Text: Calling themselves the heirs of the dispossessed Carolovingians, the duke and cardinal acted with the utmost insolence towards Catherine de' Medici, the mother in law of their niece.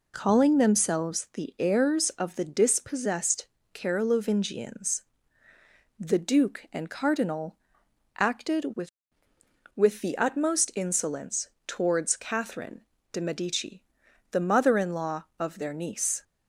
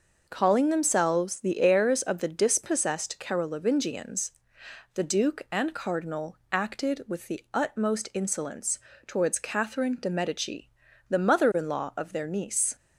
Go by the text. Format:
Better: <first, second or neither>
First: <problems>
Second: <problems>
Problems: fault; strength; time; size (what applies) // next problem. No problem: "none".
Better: second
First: pauses between "dispossessed" and "Carolovingians"; slight; at 3.4 s; 0.28 s long // pauses between "cardinal" and "acted"; noticeable; at 7.5 s; 0.60 s long // says "with" twice; at 9.7 s // pauses between "insolence" and "towards"; slight; at 11.4 s; 0.18 s long // pauses between "Catherine" and "de"; slight; at 12.8 s; 0.32 s long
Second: pauses between "insolence" and "towards"; slight; at 8.7 s; 0.28 s long